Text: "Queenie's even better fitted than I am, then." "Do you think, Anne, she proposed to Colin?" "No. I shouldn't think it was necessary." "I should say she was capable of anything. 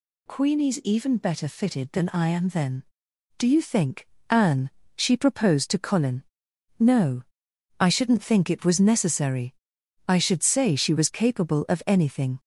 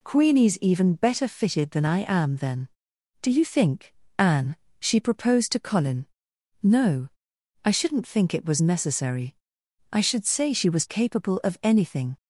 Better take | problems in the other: neither | none

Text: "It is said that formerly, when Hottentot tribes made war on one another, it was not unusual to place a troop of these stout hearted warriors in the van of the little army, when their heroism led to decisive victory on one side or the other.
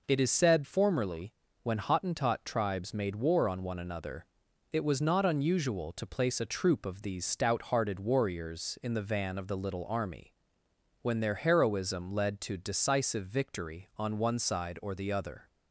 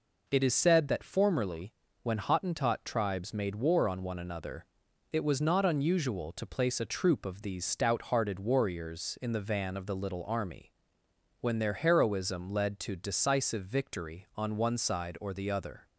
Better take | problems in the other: second | skips "that"; at 0.6 s

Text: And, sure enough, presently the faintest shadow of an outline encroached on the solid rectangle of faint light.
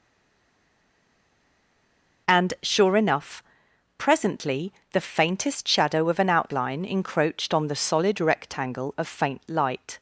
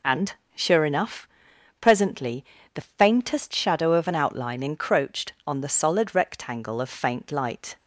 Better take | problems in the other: second | stays silent before the first word; until 2.2 s; 2.2 s long // pauses between "presently" and "the"; slight; at 4.7 s; 0.20 s long; slight in the second

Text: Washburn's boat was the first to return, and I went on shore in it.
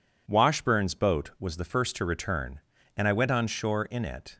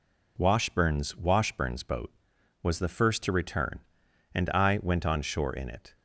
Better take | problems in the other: first | says "Washburn's" twice; at 1.1 s

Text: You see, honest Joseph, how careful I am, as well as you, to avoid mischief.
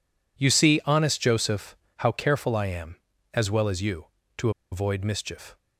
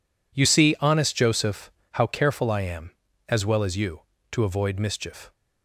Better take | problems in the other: second | pauses between "to" and "avoid"; slight; at 4.5 s; 0.21 s long

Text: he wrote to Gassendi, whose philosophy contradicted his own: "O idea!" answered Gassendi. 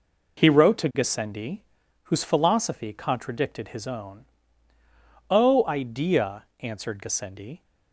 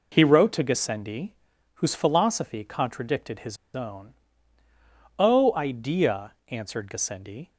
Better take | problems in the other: first | pauses between "his" and "own"; slight; at 3.5 s; 0.17 s long

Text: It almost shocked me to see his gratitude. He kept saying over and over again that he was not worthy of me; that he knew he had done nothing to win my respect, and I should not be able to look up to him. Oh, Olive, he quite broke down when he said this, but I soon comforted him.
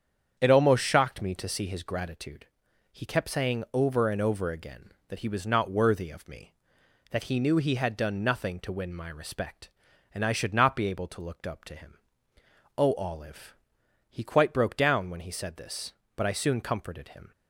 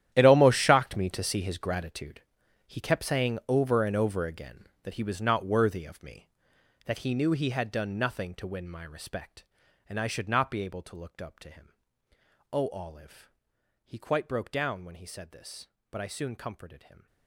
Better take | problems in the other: first | gets quieter; strong; throughout; 16 dB // starts louder than the rest; strong; until 1.1 s; 11 dB; strong in the first

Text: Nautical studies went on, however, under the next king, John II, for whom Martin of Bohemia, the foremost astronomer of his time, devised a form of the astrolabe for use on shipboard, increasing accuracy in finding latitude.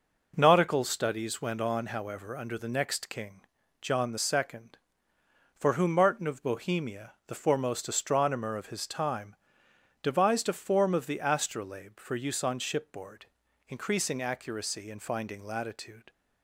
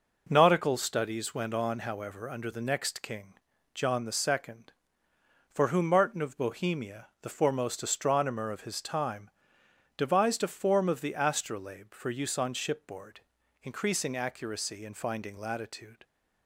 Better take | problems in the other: neither | none

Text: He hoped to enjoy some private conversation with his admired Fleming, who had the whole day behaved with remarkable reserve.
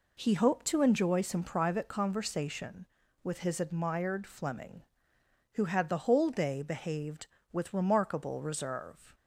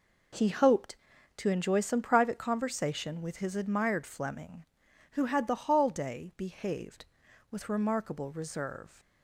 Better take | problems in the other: first | says "hall" for "whole"; at 5.6 s

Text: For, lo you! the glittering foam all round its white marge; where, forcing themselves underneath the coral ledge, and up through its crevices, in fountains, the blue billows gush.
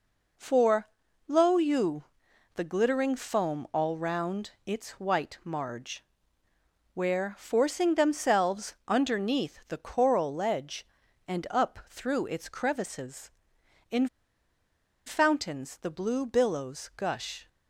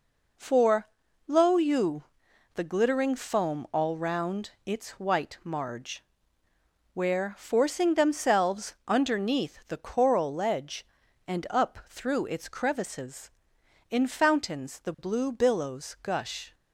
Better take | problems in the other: second | pauses between "round" and "its"; slight; at 4.5 s; 0.16 s long; slight in the second // pauses between "in" and "fountains"; noticeable; at 14.0 s; 0.97 s long

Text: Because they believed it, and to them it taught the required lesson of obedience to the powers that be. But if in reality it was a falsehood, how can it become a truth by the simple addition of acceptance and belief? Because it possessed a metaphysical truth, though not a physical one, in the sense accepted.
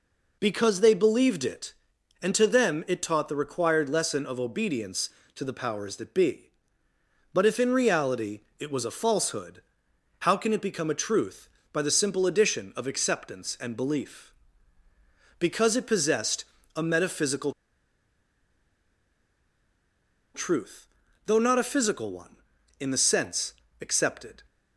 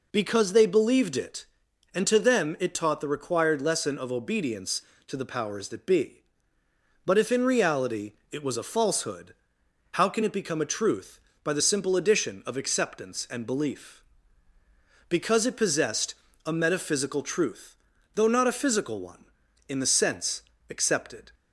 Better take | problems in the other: second | pauses between "reality" and "it"; slight; at 8.3 s; 0.18 s long; slight in the second // pauses between "possessed" and "a"; slight; at 16.4 s; 0.32 s long; slight in the second // pauses between "metaphysical" and "truth"; strong; at 17.5 s; 2.8 s long // pauses between "sense" and "accepted"; slight; at 23.5 s; 0.28 s long; slight in the second

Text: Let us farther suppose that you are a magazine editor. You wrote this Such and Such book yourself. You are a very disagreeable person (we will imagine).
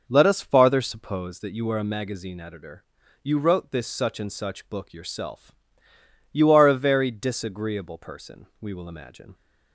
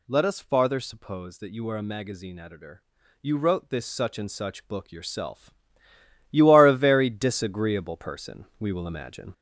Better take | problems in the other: first | gets louder; noticeable; throughout; 4.5 dB

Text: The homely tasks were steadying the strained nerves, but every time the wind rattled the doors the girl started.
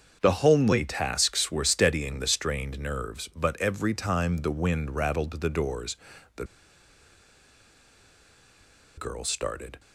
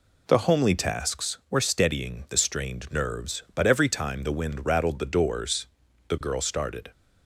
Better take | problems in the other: second | starts louder than the rest; until 1.2 s; 7 dB // pauses between "doors" and "the"; at 5.9 s; 0.40 s long; also in the second // pauses between "the" and "girl"; strong; at 6.4 s; 2.5 s long

